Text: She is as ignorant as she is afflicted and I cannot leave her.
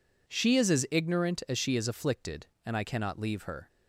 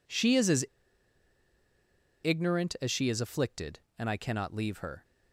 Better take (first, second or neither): first